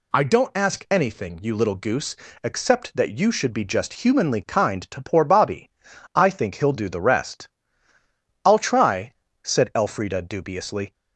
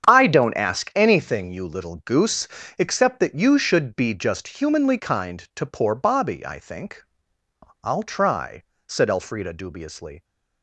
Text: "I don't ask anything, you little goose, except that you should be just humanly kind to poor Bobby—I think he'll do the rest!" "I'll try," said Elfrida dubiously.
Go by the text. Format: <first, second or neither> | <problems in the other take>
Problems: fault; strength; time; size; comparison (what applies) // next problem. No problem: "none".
first | starts louder than the rest; strong; until 1.1 s; 8.5 dB // skips "he'll do the rest"; at 7.4 s